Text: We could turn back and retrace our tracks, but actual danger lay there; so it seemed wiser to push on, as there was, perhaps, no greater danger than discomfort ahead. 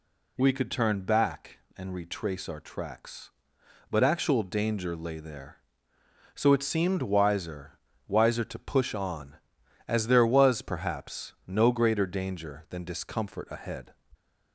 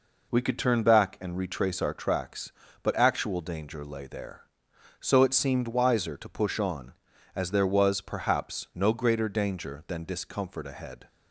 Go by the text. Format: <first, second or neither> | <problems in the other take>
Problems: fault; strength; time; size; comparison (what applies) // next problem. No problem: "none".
second | says "wiser" twice; at 8.0 s